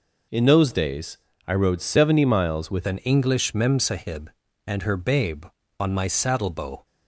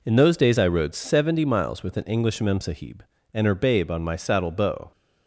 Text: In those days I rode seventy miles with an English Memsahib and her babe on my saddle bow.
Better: second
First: pauses between "days" and "I"; slight; at 1.1 s; 0.30 s long // changes voice at "an"; from 2.8 s on; 4.0 s long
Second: none

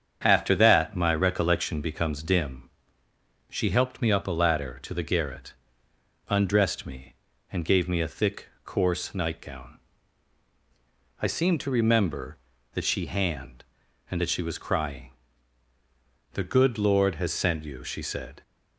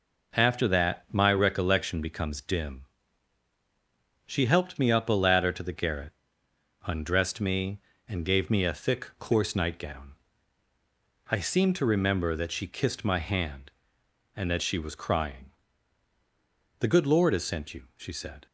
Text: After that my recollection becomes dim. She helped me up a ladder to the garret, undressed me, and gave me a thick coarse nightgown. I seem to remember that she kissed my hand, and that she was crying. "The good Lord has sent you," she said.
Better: second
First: starts louder than the rest; strong; until 1.2 s; 8 dB // pauses between "thick" and "coarse"; slight; at 8.4 s; 0.18 s long // skips "kissed my"; at 13.0 s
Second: none

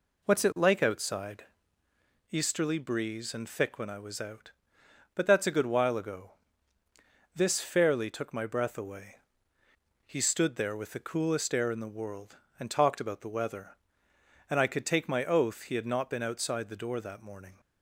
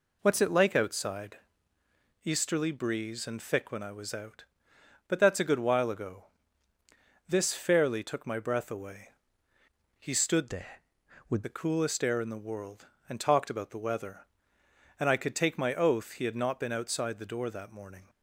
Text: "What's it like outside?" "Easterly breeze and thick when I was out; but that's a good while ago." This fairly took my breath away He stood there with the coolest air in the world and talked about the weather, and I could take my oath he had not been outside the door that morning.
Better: first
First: pauses between "away" and "He"; noticeable; at 9.1 s; 0.84 s long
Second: pauses between "away" and "He"; noticeable; at 9.1 s; 0.84 s long // changes voice from "there" to "with"; from 10.4 to 11.4 s; 1.0 s long

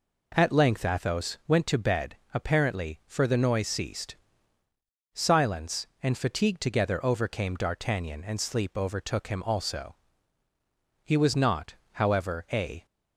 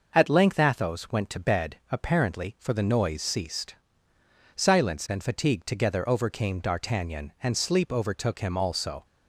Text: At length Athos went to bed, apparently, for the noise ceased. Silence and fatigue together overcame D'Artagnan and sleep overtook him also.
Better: second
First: goes on to say "He was not however a"; strong; from 11.0 s on; 1.8 s long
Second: none

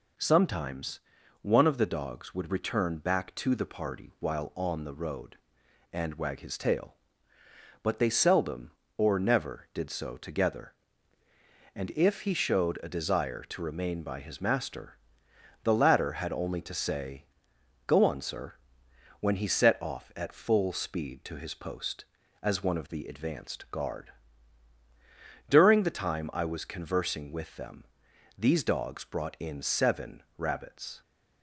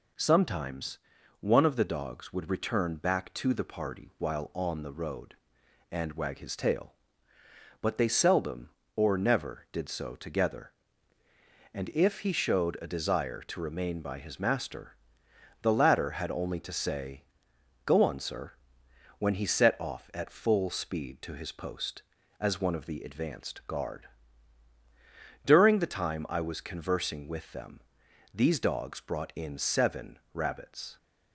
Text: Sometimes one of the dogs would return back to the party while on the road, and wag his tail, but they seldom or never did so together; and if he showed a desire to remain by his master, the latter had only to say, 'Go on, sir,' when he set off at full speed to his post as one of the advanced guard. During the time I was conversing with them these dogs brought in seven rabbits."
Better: neither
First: pauses between "Sometimes" and "one"; at 0.9 s; 0.42 s long // pauses between "them" and "these"; noticeable; at 27.8 s; 0.54 s long // pauses between "seven" and "rabbits"; slight; at 30.2 s; 0.16 s long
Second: pauses between "Sometimes" and "one"; at 0.9 s; 0.42 s long // pauses between "them" and "these"; noticeable; at 27.8 s; 0.54 s long // pauses between "seven" and "rabbits"; slight; at 30.1 s; 0.16 s long

